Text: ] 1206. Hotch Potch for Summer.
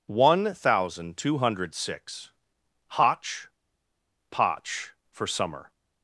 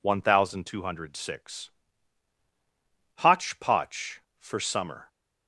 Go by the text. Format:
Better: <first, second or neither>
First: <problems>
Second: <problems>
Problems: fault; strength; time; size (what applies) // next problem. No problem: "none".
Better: second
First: pauses between "Hotch" and "Potch"; noticeable; at 3.4 s; 0.81 s long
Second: none